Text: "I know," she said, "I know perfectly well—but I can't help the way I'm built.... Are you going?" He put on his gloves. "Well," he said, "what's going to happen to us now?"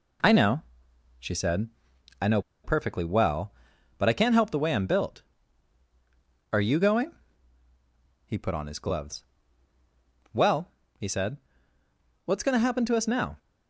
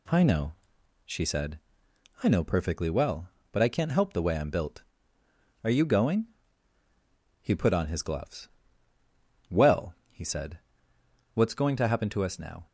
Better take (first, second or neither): second